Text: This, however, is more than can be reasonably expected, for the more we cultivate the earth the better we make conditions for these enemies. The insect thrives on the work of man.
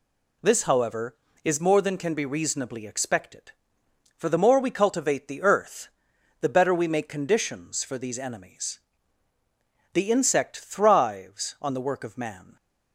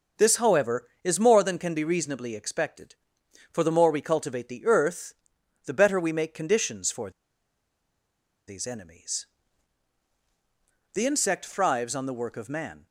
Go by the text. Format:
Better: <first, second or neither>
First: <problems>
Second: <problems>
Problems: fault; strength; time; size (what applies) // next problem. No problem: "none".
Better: first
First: pauses between "earth" and "the"; noticeable; at 5.8 s; 0.52 s long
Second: pauses between "earth" and "the"; noticeable; at 5.1 s; 0.52 s long // pauses between "for" and "these"; strong; at 7.1 s; 1.3 s long